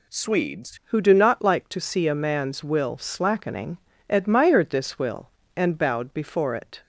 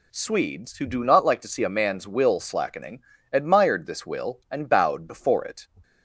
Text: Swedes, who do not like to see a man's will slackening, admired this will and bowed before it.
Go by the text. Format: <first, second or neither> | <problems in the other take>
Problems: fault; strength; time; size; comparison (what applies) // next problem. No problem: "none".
second | changes voice at "who"; from 0.8 s on; 6.0 s long